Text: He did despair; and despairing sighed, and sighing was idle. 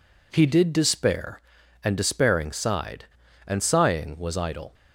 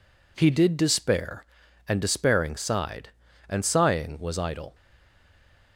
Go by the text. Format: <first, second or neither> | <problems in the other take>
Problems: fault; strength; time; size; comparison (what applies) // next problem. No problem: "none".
first | stays silent after the last word; from 4.7 s on; 1.0 s long